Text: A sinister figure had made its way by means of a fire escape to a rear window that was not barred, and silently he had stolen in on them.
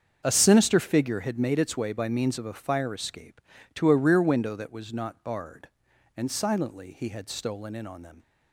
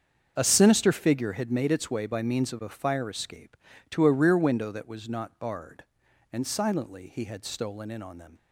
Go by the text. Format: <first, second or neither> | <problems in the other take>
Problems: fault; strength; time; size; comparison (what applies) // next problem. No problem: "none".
neither | starts louder than the rest; the same in both